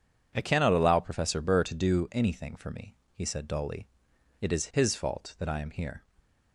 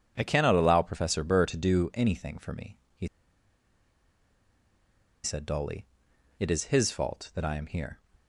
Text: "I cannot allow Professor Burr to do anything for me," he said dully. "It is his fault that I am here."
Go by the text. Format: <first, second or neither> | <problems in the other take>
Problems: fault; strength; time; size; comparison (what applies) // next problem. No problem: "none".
first | pauses between "he" and "said"; strong; at 3.0 s; 2.1 s long